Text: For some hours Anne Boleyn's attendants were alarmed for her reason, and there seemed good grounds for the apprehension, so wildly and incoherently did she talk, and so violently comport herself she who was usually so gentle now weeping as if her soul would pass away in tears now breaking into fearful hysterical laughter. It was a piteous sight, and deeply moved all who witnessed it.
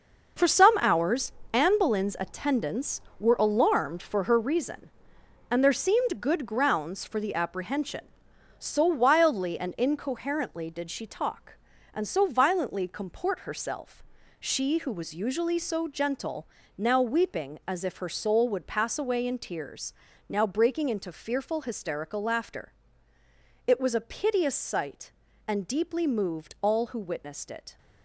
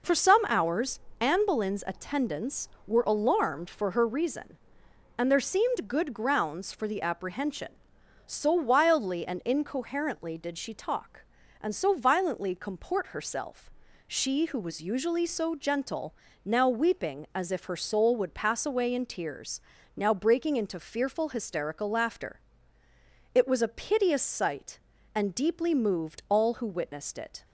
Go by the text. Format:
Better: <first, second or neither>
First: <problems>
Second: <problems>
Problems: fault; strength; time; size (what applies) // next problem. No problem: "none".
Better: second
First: gets quieter; strong; throughout; 9.5 dB // pauses between "hours" and "Anne"; slight; at 1.3 s; 0.20 s long // pauses between "herself" and "she"; slight; at 14.0 s; 0.36 s long // pauses between "gentle" and "now"; slight; at 16.4 s; 0.32 s long // pauses between "tears" and "now"; at 19.9 s; 0.38 s long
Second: pauses between "hours" and "Anne"; slight; at 0.9 s; 0.20 s long // pauses between "herself" and "she"; slight; at 13.7 s; 0.36 s long // pauses between "gentle" and "now"; slight; at 16.1 s; 0.32 s long // pauses between "tears" and "now"; at 19.5 s; 0.38 s long